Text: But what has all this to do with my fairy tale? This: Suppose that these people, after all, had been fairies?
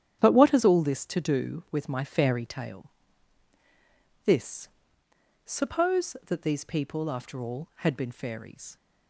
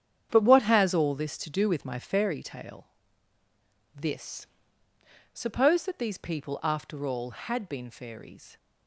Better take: neither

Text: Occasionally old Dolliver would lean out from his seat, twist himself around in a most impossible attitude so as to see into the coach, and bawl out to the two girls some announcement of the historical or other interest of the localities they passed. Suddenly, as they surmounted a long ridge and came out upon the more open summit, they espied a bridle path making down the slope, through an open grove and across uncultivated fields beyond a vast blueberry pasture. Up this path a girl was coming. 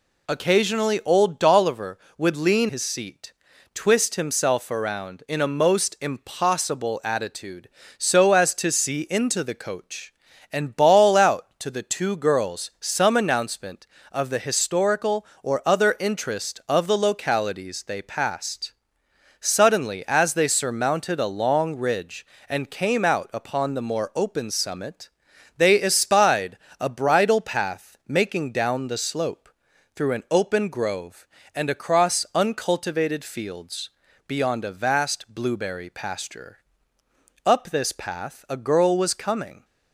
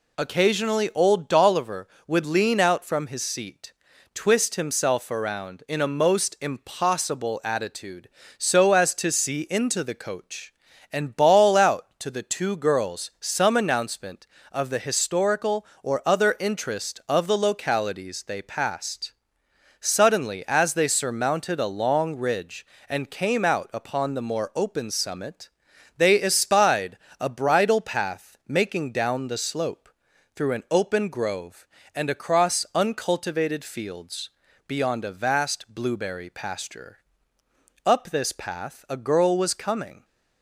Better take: second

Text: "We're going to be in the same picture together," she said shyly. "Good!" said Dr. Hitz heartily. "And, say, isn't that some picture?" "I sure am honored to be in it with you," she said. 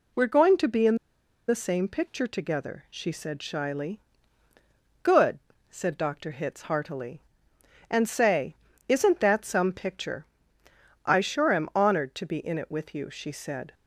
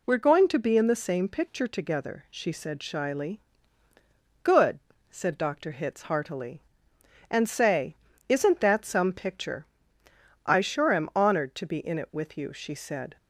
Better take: second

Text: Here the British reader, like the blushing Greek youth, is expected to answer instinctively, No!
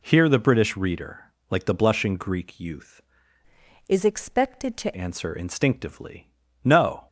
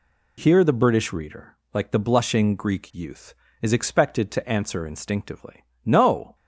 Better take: second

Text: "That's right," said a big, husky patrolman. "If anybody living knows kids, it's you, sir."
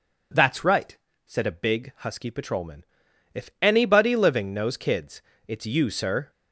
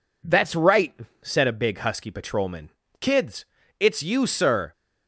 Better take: first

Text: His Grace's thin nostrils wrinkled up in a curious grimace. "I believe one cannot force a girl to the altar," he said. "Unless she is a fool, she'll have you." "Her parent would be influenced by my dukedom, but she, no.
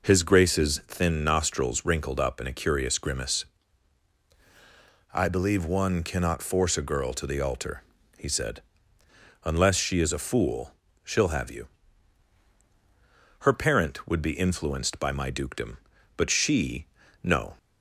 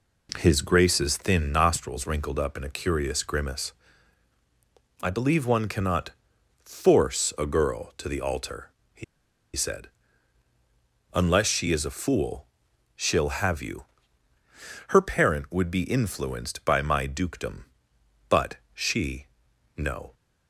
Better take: first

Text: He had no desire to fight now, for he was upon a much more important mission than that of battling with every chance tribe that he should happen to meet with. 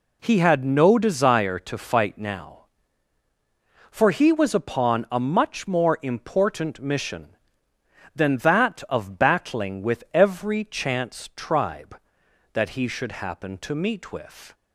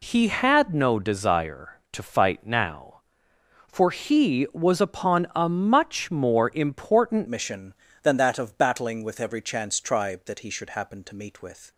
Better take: first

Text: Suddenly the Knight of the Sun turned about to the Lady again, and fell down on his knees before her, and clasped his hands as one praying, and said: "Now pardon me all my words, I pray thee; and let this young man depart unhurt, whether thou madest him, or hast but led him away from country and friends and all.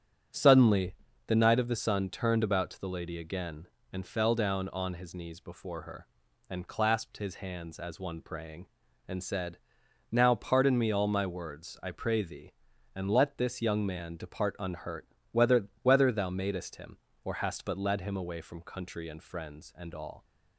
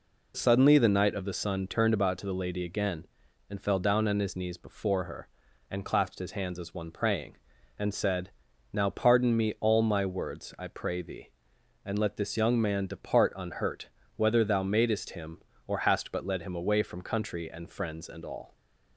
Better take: second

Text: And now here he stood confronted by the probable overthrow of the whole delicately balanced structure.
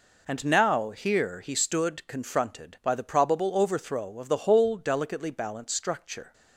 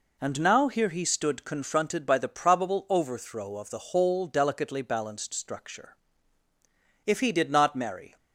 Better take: first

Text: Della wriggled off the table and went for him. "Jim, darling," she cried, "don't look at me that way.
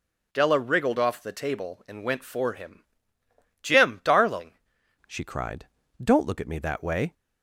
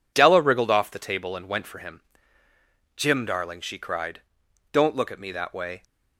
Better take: second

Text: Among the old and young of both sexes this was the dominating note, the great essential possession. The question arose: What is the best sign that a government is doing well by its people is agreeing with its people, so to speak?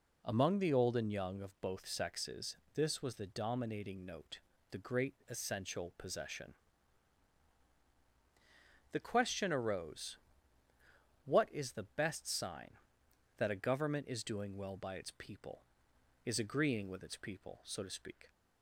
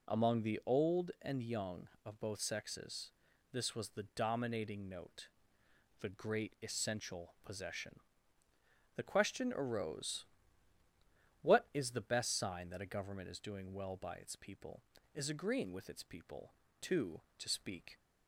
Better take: first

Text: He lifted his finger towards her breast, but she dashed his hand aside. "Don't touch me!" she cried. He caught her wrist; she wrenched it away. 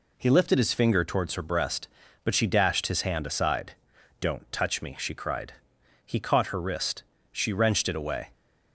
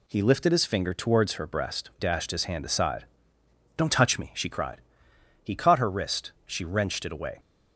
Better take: first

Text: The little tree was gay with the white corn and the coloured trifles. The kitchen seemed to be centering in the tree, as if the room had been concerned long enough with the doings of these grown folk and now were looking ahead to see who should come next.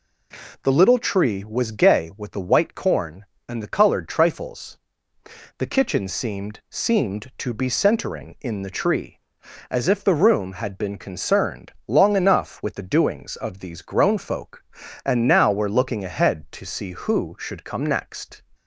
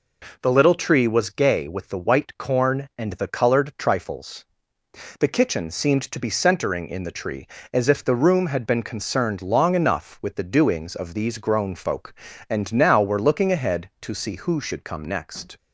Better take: second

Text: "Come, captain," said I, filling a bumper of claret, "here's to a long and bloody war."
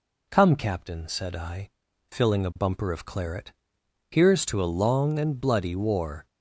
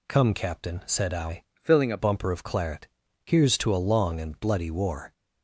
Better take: first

